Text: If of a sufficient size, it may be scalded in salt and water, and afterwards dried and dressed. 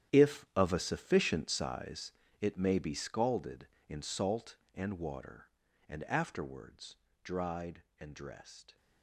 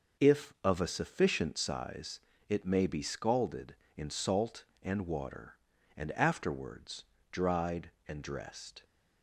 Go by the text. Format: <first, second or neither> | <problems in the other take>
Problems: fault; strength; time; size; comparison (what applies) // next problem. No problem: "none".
second | gets quieter; strong; throughout; 14 dB // pauses between "afterwards" and "dried"; slight; at 6.9 s; 0.28 s long; slight in the second